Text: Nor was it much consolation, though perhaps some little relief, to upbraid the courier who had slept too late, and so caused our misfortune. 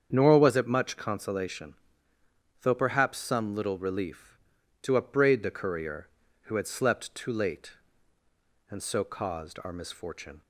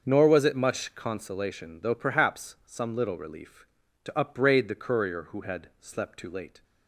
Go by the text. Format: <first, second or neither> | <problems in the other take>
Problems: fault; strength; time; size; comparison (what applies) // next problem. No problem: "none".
first | starts louder than the rest; until 1.0 s; 6.5 dB; strong in the first // stops before "and so caused our misfortune"; at 6.6 s